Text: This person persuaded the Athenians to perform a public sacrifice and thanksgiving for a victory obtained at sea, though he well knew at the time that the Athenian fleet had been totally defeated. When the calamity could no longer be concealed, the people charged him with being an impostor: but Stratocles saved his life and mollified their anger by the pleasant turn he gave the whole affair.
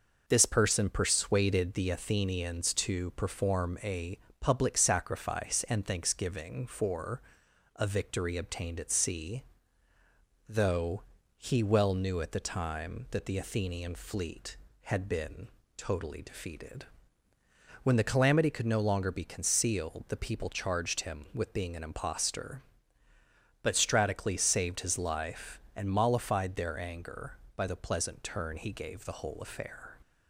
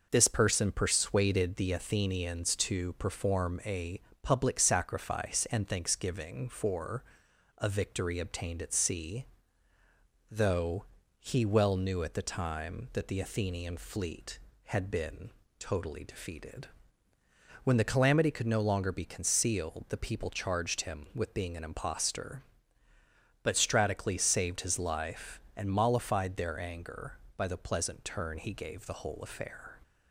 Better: neither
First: pauses between "a" and "public"; slight; at 4.1 s; 0.22 s long // pauses between "for" and "a"; noticeable; at 7.2 s; 0.56 s long // pauses between "though" and "he"; slight; at 11.0 s; 0.34 s long // pauses between "been" and "totally"; slight; at 15.4 s; 0.28 s long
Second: pauses between "a" and "public"; slight; at 4.0 s; 0.22 s long // pauses between "for" and "a"; noticeable; at 7.0 s; 0.56 s long // pauses between "though" and "he"; slight; at 10.8 s; 0.34 s long // pauses between "been" and "totally"; slight; at 15.3 s; 0.28 s long

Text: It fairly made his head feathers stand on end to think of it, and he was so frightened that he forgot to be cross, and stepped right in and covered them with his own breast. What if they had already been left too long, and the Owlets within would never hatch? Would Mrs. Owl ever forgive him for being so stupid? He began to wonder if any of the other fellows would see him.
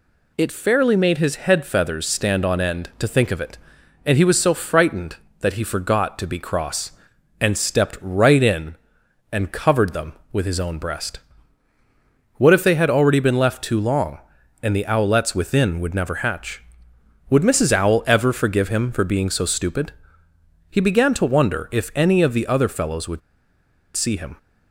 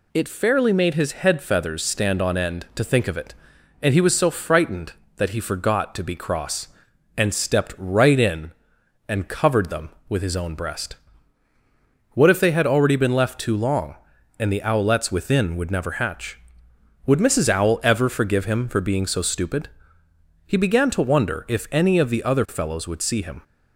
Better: second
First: pauses between "would" and "see"; noticeable; at 23.2 s; 0.75 s long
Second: none

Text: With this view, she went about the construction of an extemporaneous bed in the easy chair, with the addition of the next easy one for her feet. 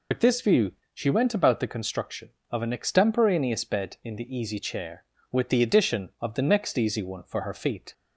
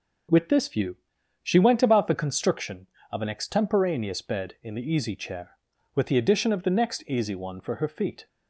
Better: second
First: loses the start of "With"; at 0.1 s; 80 ms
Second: none

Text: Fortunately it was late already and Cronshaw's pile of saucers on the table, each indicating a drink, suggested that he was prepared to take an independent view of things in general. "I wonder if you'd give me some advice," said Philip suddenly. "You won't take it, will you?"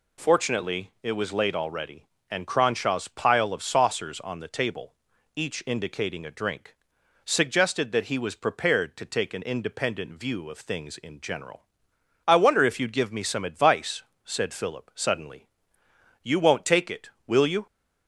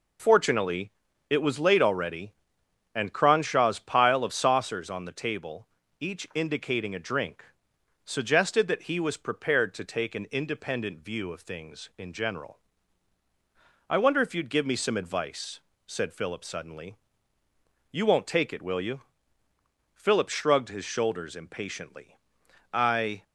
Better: first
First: none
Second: pauses between "Fortunately" and "it"; at 0.9 s; 0.40 s long // goes on to say "Philip shrugged his shoulders impatiently I"; strong; from 19.9 s on; 3.2 s long

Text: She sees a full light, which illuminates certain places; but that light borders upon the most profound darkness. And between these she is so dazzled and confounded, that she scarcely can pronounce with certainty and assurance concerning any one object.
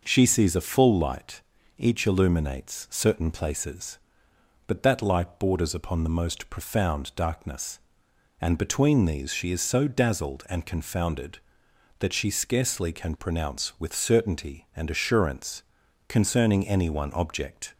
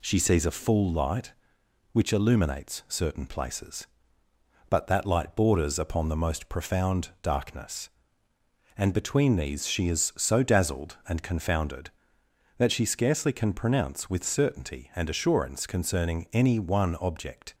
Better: second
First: says "each" for "which"; at 1.7 s // pauses between "assurance" and "concerning"; at 15.6 s; 0.44 s long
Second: none

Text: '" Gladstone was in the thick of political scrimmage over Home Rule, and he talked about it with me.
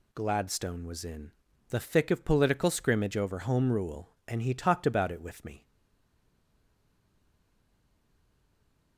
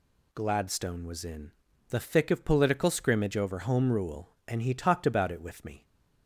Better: second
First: pauses between "in" and "the"; at 1.3 s; 0.40 s long // stays silent after the last word; strong; from 5.6 s on; 3.3 s long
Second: pauses between "in" and "the"; at 1.5 s; 0.40 s long

